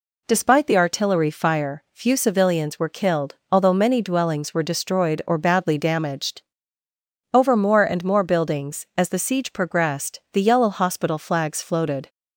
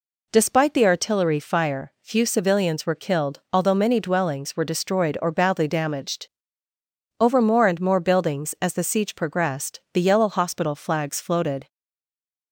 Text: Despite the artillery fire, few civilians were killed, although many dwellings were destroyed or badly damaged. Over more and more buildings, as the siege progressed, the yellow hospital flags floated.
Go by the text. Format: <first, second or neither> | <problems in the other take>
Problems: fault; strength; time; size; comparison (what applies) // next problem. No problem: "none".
first | stays silent after the last word; slight; from 11.6 s on; 0.9 s long